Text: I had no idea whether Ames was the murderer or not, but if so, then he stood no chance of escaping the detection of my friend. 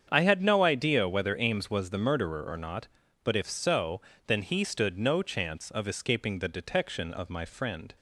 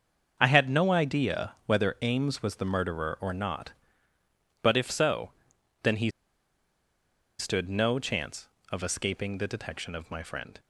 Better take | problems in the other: first | starts louder than the rest; until 1.4 s; 6.5 dB; strong in the first // pauses between "he" and "stood"; strong; at 6.0 s; 1.2 s long

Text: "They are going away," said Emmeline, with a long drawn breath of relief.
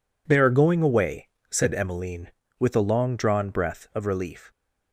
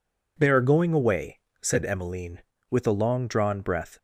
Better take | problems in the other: first | stops before "of relief"; at 3.9 s

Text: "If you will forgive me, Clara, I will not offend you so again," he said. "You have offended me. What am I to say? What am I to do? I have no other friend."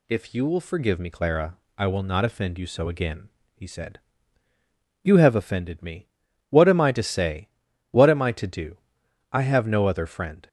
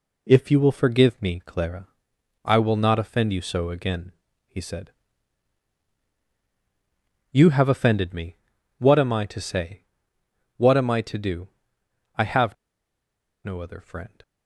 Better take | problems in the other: first | pauses between "have" and "no"; noticeable; at 12.5 s; 0.90 s long

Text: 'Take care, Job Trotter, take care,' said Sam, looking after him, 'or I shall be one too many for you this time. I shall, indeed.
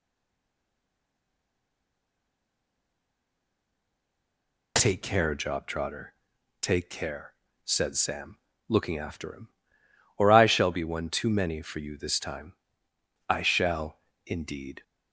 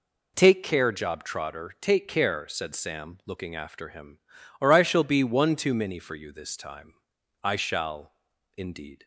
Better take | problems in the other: second | stays silent before the first word; strong; until 4.7 s; 4.7 s long

